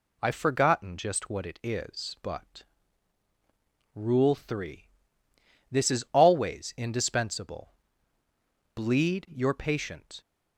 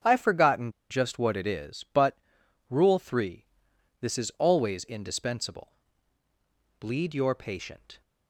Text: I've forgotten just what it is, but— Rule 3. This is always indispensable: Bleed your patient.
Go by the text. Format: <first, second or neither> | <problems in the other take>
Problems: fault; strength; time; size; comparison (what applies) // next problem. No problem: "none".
first | starts louder than the rest; strong; until 1.2 s; 7.5 dB // pauses between "forgotten" and "just"; slight; at 0.7 s; 0.19 s long